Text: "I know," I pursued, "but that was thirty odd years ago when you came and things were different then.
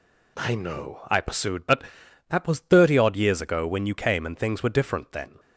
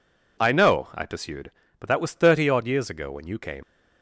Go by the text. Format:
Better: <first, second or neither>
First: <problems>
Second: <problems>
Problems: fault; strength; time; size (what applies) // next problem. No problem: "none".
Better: first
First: none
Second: stops before "and things were different then"; at 3.6 s